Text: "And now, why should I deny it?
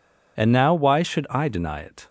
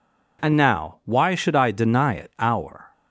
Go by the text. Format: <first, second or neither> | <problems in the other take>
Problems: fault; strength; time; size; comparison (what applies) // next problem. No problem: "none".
first | goes on to say "our"; from 2.3 s on; 0.54 s long